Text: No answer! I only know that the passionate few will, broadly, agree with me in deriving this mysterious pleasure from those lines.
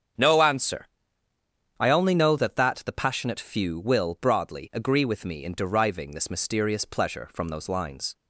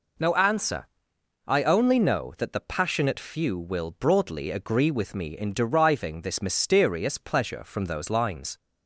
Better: second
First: starts louder than the rest; strong; until 2.1 s; 7.5 dB // says "that" twice; at 2.5 s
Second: none

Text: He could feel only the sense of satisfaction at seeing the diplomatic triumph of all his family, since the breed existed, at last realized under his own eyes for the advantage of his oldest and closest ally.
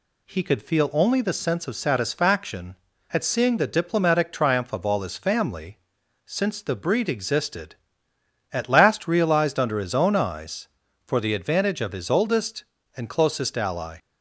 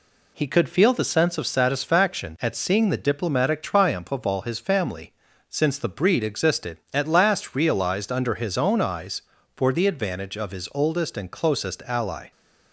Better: first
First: none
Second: skips "only"; at 0.9 s

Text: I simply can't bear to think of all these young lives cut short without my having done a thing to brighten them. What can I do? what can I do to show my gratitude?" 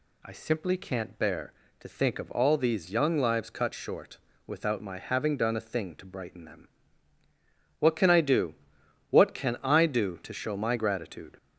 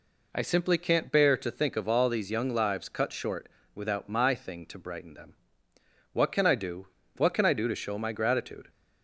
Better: first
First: pauses between "short" and "without"; slight; at 4.1 s; 0.28 s long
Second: pauses between "short" and "without"; slight; at 3.4 s; 0.26 s long // skips "having done a"; at 4.3 s

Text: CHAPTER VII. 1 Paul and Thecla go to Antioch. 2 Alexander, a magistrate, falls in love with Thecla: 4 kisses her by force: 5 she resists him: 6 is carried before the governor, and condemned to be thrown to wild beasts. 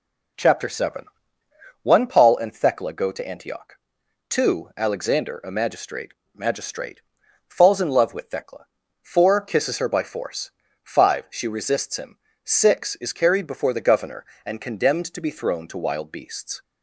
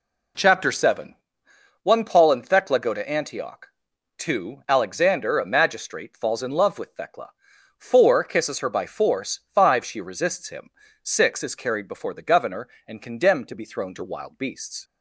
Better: second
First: says "magistrate" twice; at 6.3 s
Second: none

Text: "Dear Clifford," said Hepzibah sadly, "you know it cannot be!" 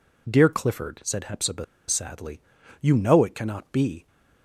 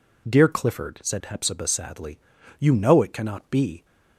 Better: second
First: pauses between "Hepzibah" and "sadly"; slight; at 1.6 s; 0.23 s long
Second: none

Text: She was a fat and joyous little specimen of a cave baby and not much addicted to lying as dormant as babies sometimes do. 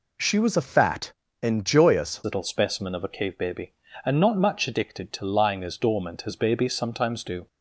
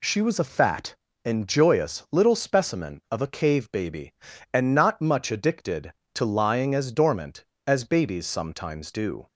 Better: second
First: changes voice at "little"; from 2.2 s on; 5.2 s long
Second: none

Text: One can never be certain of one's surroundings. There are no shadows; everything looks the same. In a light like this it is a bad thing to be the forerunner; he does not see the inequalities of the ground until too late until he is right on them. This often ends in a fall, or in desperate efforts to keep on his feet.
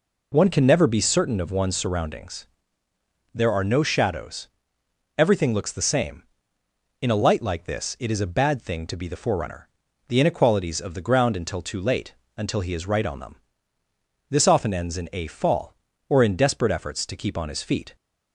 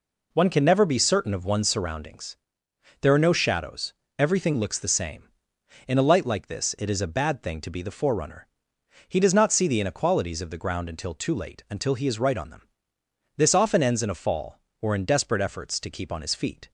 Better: second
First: skips "he does not see"; at 9.8 s // pauses between "late" and "until"; slight; at 12.1 s; 0.20 s long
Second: none

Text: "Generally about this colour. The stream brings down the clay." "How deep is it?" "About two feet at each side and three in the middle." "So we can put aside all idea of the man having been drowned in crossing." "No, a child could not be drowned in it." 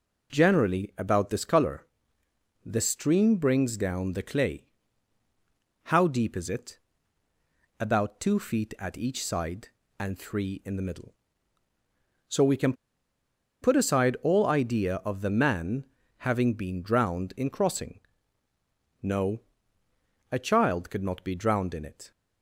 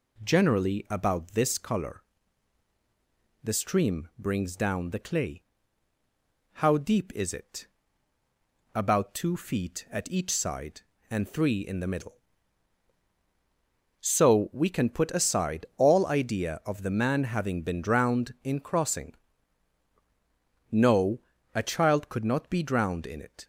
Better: second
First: pauses between "can" and "put"; noticeable; at 12.7 s; 0.88 s long // pauses between "man" and "having"; slight; at 15.8 s; 0.30 s long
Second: none

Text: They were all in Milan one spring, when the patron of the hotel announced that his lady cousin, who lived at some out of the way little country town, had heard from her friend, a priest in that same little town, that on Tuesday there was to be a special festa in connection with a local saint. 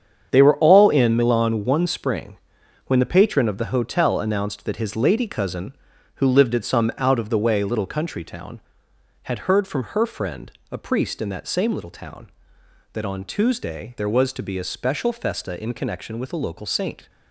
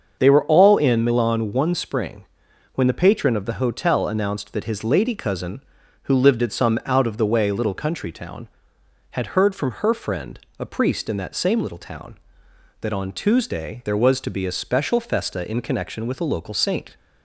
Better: second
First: gets quieter; strong; throughout; 9.5 dB // starts louder than the rest; strong; until 1.3 s; 8 dB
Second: starts louder than the rest; until 1.1 s; 6.5 dB

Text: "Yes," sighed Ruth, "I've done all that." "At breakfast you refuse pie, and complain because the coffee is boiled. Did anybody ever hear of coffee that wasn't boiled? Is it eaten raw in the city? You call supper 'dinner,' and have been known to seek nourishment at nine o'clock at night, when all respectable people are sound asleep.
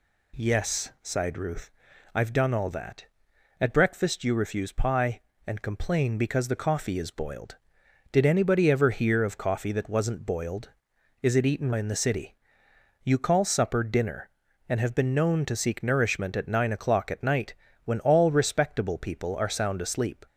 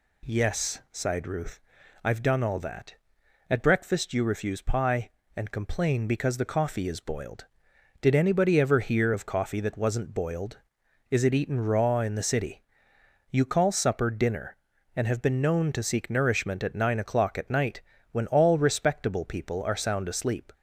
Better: second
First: skips "raw"; at 11.7 s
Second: none

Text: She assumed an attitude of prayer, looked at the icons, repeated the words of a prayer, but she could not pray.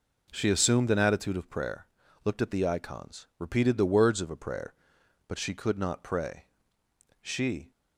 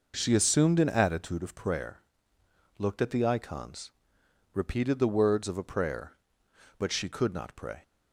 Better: second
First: goes on to say "She"; from 7.2 s on; 0.50 s long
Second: none

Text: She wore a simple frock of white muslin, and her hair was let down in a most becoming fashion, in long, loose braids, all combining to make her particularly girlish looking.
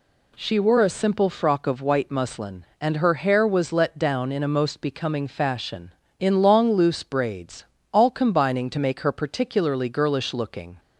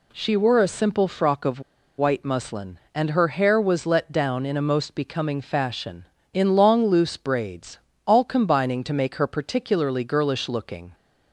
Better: first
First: none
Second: pauses between "of" and "white"; at 1.5 s; 0.38 s long

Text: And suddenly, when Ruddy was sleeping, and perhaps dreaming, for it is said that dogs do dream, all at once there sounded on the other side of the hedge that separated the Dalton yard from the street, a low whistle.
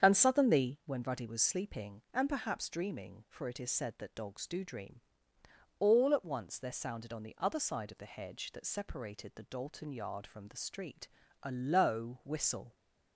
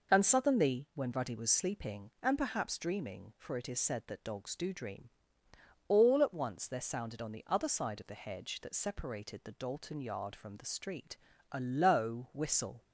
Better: second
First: starts louder than the rest; strong; until 1.0 s; 7.5 dB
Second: none

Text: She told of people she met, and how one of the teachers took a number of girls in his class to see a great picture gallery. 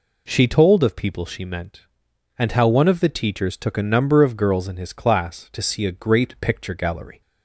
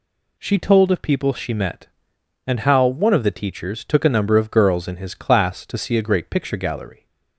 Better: second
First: says "meant" for "met"; at 1.4 s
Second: none

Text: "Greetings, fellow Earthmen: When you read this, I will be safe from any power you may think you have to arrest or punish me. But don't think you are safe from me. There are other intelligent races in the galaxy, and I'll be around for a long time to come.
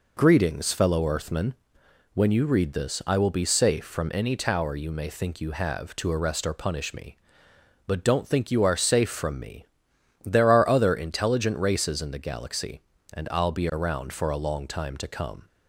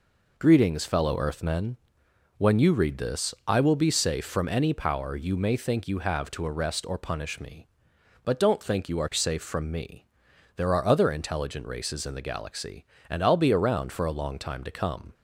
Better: second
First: says "tower" for "power"; at 4.3 s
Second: none

